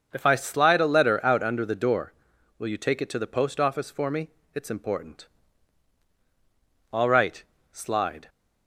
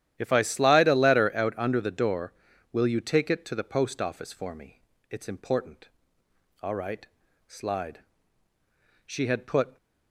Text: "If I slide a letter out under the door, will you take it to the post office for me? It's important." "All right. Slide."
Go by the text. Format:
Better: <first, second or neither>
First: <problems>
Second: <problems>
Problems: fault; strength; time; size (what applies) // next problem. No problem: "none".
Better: first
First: starts louder than the rest; until 1.1 s; 6 dB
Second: starts louder than the rest; strong; until 1.1 s; 11 dB // goes on to say "She had put"; noticeable; from 9.0 s on; 0.72 s long